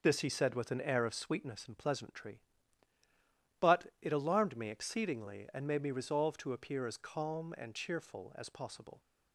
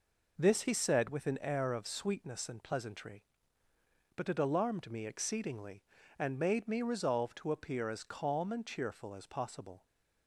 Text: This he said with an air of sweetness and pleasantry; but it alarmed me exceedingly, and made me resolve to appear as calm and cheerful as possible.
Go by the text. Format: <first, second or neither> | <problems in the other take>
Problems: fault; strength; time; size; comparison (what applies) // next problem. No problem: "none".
neither | none